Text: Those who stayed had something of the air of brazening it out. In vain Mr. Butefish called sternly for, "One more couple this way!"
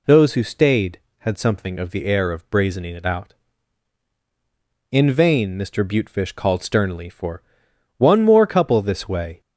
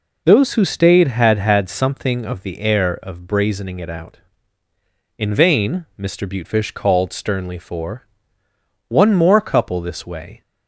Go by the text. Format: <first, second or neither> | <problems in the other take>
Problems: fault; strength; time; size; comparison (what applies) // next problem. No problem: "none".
first | says "had" twice; at 1.3 s